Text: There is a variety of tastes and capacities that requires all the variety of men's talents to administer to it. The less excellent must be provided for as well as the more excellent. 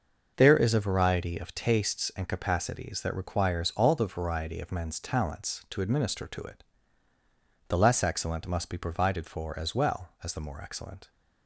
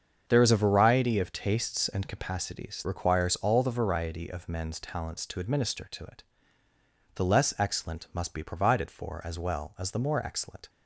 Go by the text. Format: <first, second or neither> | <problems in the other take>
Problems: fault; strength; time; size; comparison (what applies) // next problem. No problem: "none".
first | starts louder than the rest; until 1.2 s; 7 dB // skips "that"; at 2.8 s